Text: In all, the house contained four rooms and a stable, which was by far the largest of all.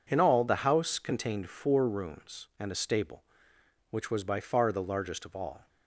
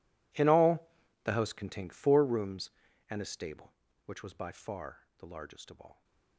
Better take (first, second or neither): first